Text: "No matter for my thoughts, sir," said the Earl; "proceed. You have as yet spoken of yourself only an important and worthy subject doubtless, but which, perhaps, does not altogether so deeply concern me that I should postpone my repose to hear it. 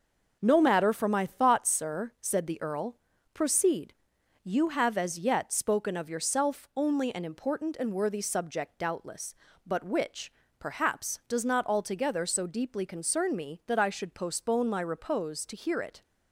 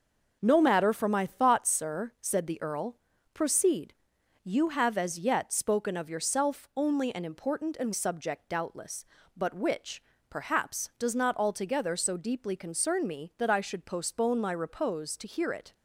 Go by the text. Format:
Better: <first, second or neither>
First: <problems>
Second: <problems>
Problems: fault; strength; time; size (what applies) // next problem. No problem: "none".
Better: first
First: none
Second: skips "worthy"; at 7.9 s